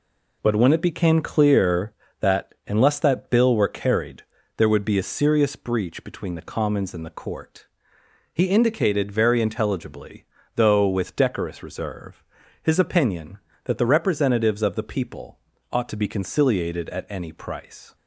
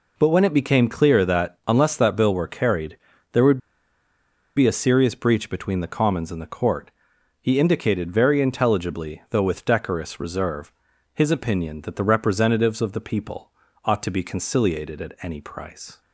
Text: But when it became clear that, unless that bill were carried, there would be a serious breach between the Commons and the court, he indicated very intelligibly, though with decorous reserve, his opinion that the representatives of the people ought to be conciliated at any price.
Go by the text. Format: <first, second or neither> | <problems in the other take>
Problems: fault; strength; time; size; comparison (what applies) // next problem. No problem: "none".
first | pauses between "would" and "be"; at 3.5 s; 0.98 s long // pauses between "people" and "ought"; slight; at 13.5 s; 0.34 s long; slight in the first